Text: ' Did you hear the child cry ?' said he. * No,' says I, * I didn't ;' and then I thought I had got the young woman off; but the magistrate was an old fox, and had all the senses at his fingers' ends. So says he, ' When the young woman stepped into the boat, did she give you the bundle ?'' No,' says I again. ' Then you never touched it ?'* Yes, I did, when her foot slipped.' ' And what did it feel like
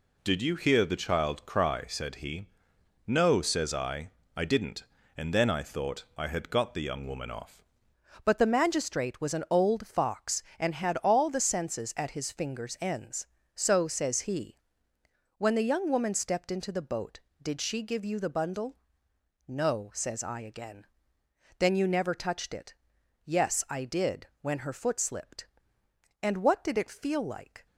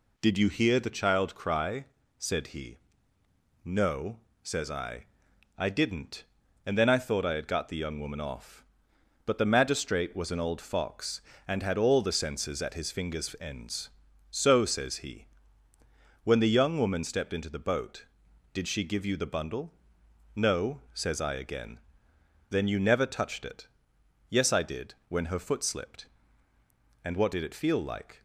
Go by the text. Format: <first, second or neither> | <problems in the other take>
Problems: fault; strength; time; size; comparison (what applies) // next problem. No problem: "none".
second | changes voice at "but"; from 8.2 s on; 19.4 s long